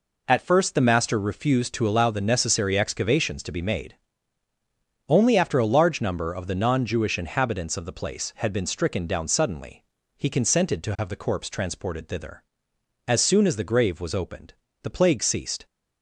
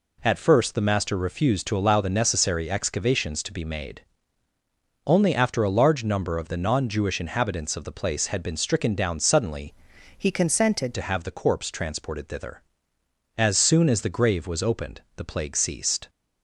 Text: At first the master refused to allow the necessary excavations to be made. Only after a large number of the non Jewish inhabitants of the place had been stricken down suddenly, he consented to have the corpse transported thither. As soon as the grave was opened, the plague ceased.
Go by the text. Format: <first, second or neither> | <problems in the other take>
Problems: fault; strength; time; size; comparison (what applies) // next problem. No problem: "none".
first | changes voice from "he" to "consented"; from 10.1 to 10.9 s; 0.8 s long